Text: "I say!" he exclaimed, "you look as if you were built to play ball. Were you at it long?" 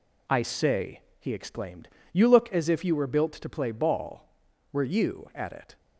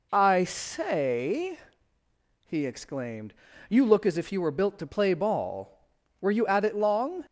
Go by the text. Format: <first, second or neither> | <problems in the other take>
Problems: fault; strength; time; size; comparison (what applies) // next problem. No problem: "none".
second | stops before "long"; at 5.7 s